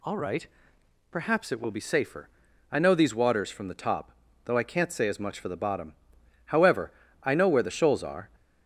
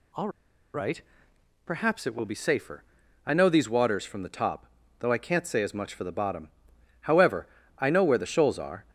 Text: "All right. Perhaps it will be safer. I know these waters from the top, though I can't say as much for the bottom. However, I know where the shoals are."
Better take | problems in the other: first | pauses between "All" and "right"; at 0.2 s; 0.45 s long

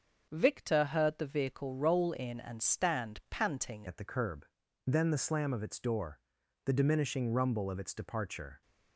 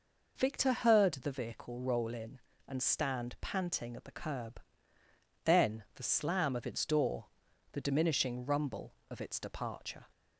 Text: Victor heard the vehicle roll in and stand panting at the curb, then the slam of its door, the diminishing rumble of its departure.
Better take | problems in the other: second | starts louder than the rest; until 1.3 s; 6 dB // changes voice at "at"; from 3.8 s on; 4.8 s long

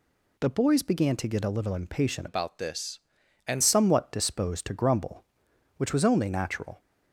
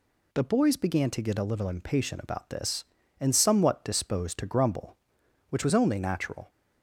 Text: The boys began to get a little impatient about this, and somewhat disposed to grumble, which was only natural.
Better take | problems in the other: second | changes voice from "about" to "and"; from 2.2 to 3.6 s; 1.4 s long

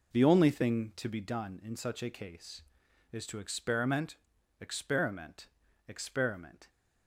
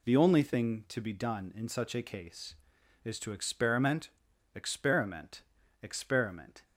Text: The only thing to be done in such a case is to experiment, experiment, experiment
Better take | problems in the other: second | starts louder than the rest; noticeable; until 1.4 s; 4.5 dB

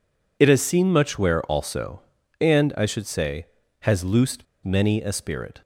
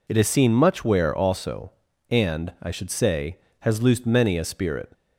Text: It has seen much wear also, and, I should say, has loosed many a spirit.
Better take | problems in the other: second | pauses between "loosed" and "many"; slight; at 4.4 s; 0.19 s long

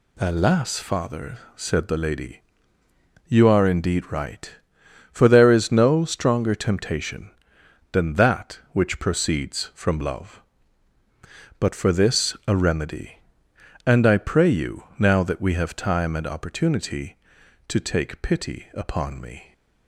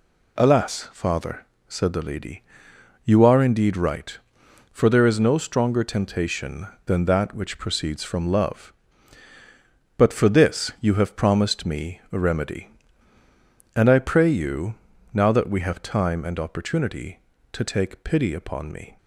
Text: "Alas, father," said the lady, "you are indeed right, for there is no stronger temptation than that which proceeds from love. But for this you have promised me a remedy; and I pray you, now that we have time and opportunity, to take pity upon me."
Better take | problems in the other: second | skips "you have promised me"; at 12.4 s

